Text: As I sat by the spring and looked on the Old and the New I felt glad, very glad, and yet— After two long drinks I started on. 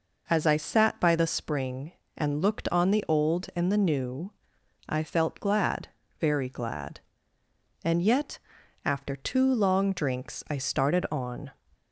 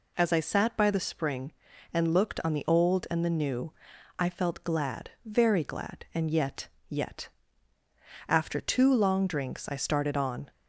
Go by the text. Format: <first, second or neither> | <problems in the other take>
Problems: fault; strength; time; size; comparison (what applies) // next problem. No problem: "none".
first | pauses between "New" and "I"; noticeable; at 3.7 s; 0.48 s long; noticeable in the first // says "yet" twice; at 6.8 s